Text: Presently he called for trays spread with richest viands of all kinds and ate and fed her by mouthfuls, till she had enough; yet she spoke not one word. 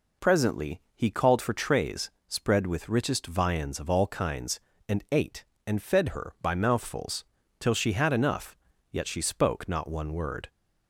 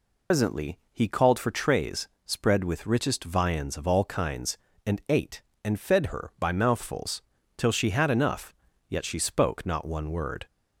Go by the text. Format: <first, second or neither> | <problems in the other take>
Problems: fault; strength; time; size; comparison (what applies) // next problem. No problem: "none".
first | loses the start of "Presently"; at 0.3 s; 120 ms // pauses between "trays" and "spread"; slight; at 2.0 s; 0.18 s long; slight in the first